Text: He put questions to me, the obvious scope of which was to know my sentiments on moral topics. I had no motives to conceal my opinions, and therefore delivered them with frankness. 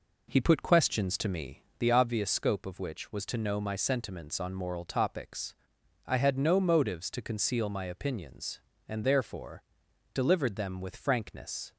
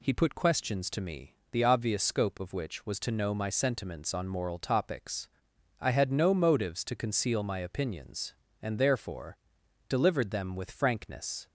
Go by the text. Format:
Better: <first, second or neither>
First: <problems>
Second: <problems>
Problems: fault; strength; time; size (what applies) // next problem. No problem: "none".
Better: second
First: starts louder than the rest; noticeable; until 2.0 s; 4 dB // pauses between "therefore" and "delivered"; noticeable; at 9.6 s; 0.49 s long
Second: pauses between "therefore" and "delivered"; noticeable; at 9.3 s; 0.50 s long